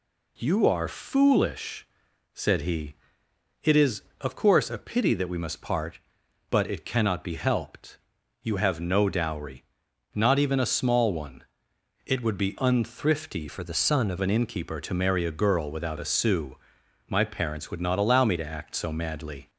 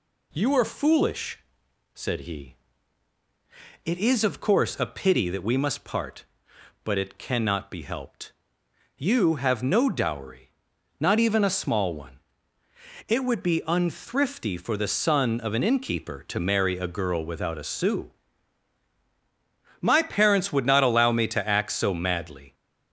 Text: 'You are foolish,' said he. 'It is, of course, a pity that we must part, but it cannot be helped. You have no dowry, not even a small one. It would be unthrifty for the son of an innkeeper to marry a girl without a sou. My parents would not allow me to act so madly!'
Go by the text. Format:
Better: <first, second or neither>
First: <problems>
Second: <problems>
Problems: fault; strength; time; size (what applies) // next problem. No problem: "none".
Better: second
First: changes voice from "for" to "of"; from 13.4 to 14.1 s; 0.7 s long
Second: none